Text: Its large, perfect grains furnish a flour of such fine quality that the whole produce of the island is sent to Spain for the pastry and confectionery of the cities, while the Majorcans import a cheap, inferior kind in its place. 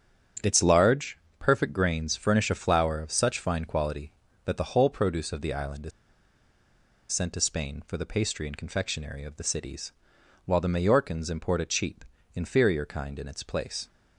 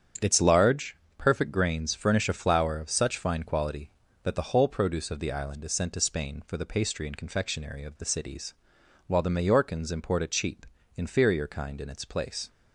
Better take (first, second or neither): second